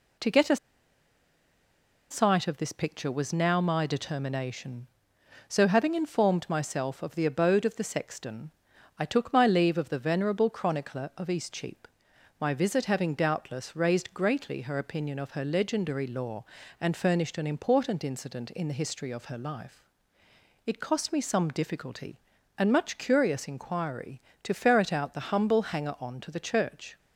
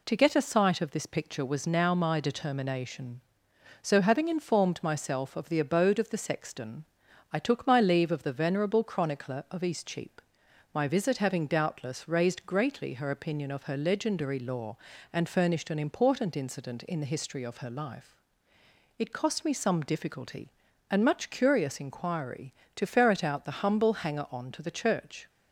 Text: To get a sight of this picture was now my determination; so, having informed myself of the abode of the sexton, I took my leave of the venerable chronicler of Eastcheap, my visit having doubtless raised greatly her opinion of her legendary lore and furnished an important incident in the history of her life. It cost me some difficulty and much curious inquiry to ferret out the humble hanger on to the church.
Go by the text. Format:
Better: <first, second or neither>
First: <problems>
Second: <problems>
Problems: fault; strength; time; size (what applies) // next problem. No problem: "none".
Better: second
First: pauses between "a" and "sight"; strong; at 0.5 s; 1.5 s long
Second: none